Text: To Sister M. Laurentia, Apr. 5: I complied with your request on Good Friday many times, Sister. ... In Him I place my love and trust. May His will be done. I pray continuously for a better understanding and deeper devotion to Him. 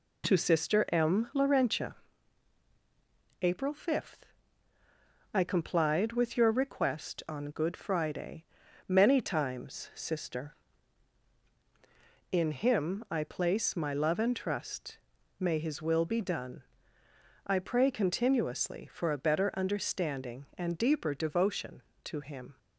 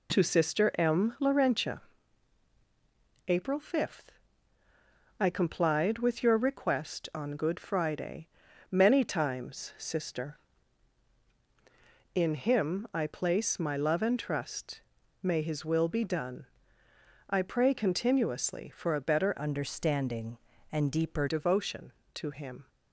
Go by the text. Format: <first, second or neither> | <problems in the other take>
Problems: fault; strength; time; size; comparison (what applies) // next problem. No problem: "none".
first | pauses between "Friday" and "many"; at 8.2 s; 0.42 s long; also in the first // changes voice from "understanding" to "deeper"; from 19.4 to 21.2 s; 1.8 s long